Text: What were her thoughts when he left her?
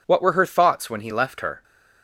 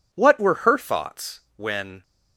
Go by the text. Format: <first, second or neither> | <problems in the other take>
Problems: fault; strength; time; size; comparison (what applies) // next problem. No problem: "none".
first | pauses between "thoughts" and "when"; slight; at 1.3 s; 0.16 s long // stops before "he left her"; at 2.0 s